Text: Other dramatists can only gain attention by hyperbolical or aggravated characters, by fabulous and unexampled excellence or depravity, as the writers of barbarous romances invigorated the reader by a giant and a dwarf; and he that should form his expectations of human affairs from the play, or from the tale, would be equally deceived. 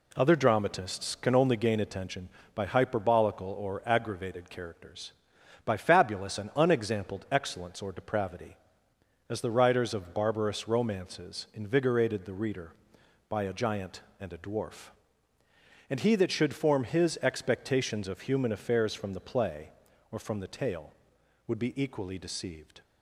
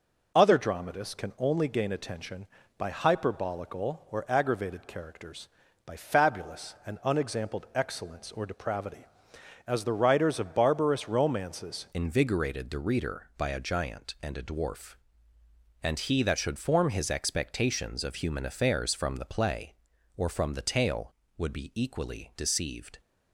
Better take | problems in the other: first | changes voice at "invigorated"; from 11.9 s on; 11.0 s long

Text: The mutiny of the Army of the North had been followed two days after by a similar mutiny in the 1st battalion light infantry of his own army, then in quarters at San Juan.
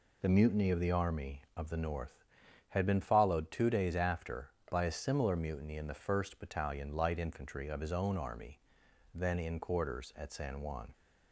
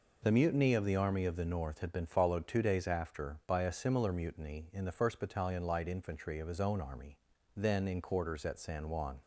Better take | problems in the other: neither | none

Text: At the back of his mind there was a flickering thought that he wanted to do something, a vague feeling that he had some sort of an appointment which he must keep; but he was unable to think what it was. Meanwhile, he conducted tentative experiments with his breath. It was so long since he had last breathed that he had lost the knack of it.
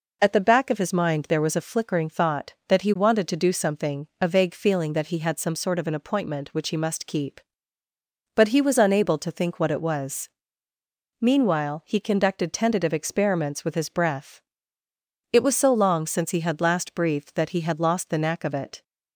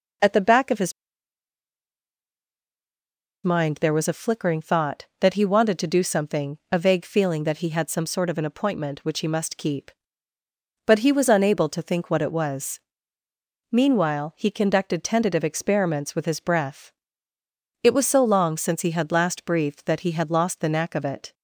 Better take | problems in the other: first | pauses between "his" and "mind"; strong; at 0.9 s; 2.5 s long

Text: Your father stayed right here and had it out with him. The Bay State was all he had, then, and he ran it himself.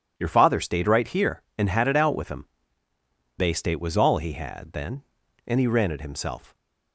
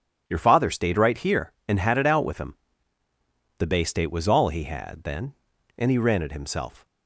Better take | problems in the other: second | skips "The"; at 2.9 s

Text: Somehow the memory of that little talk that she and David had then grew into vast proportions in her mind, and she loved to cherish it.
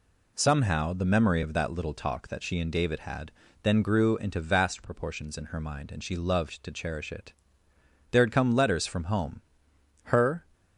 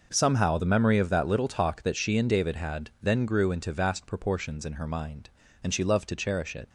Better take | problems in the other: second | pauses between "had" and "then"; slight; at 3.3 s; 0.30 s long // goes on to say "There had come letters from home Her"; strong; from 8.1 s on; 2.3 s long

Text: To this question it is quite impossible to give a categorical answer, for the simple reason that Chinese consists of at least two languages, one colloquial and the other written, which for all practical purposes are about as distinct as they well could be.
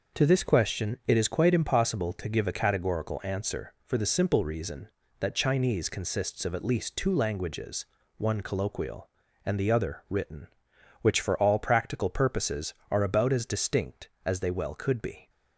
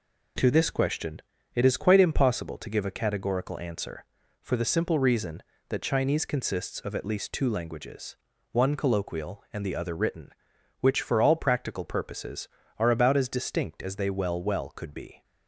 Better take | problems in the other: first | pauses between "question" and "it"; slight; at 1.2 s; 0.32 s long // says "well" twice; at 14.3 s

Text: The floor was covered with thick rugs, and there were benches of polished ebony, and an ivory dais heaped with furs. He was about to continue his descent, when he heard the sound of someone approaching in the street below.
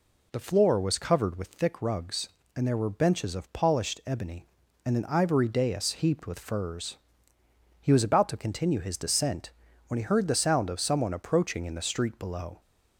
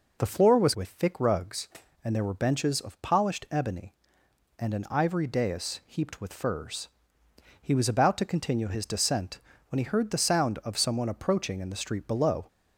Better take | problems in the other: first | skips "covered"; at 0.7 s

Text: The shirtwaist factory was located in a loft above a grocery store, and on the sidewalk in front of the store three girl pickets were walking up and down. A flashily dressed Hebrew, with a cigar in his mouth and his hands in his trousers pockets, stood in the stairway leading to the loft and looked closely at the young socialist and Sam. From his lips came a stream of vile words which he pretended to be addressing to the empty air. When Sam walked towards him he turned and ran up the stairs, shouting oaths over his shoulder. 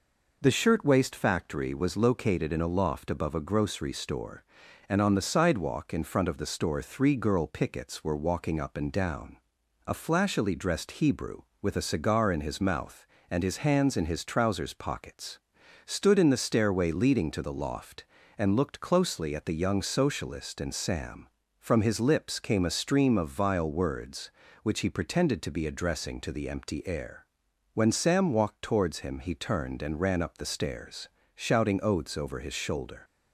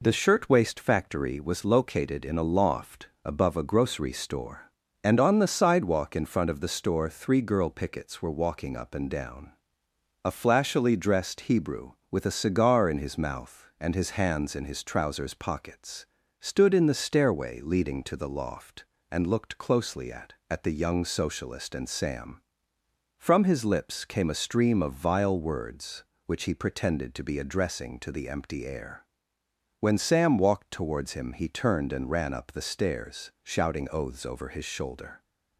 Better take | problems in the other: first | pauses between "loft" and "above"; slight; at 3.0 s; 0.18 s long // says "at" twice; at 20.5 s

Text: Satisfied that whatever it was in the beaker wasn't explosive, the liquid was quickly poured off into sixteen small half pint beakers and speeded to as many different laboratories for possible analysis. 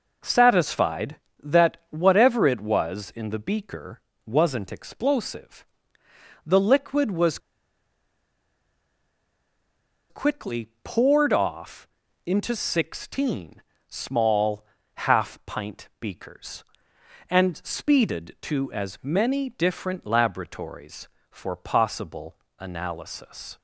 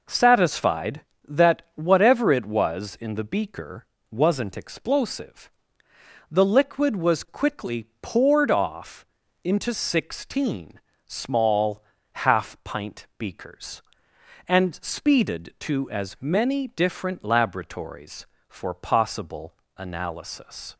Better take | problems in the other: second | pauses between "beaker" and "wasn't"; slight; at 3.9 s; 0.26 s long; slight in the second // pauses between "was" and "quickly"; strong; at 7.3 s; 2.7 s long // pauses between "off" and "into"; at 11.8 s; 0.38 s long; also in the second // pauses between "sixteen" and "small"; slight; at 13.6 s; 0.28 s long; slight in the second // pauses between "small" and "half"; slight; at 14.6 s; 0.30 s long; slight in the second // pauses between "possible" and "analysis"; slight; at 22.3 s; 0.22 s long; slight in the second

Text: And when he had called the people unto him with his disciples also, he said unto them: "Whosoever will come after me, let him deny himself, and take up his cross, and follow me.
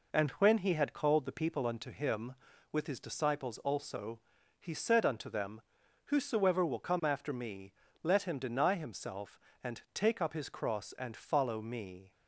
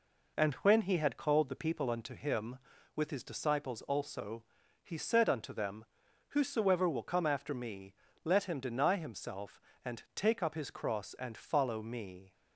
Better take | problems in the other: neither | none

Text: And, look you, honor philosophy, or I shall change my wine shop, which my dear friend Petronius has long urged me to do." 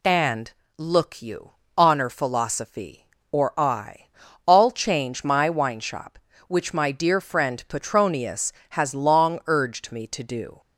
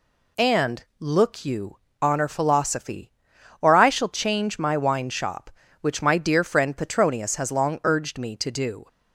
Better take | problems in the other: second | says "all" for "shall"; at 4.4 s

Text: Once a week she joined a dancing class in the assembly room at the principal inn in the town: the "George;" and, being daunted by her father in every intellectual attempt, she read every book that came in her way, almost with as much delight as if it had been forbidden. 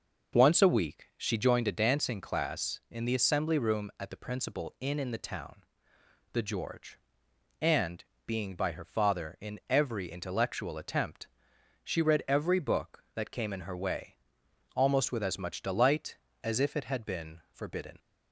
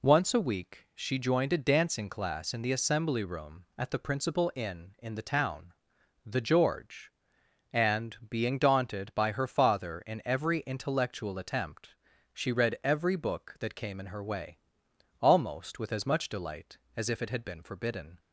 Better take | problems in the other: second | skips "daunted"; at 8.5 s

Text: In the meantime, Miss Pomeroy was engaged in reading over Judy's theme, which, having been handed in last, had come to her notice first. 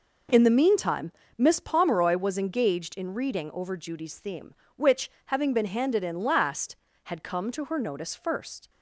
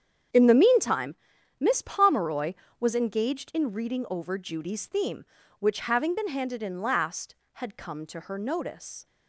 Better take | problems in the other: first | starts louder than the rest; strong; until 1.7 s; 8.5 dB // stops before "first"; at 9.0 s

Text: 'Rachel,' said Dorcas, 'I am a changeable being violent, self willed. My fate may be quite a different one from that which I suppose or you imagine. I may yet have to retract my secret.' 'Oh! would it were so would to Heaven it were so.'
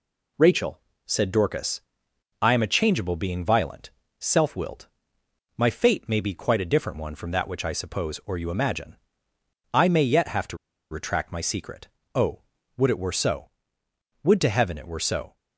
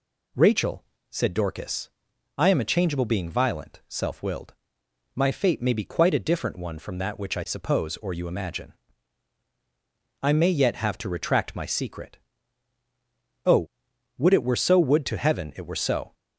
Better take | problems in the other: second | pauses between "to" and "retract"; slight; at 10.5 s; 0.35 s long

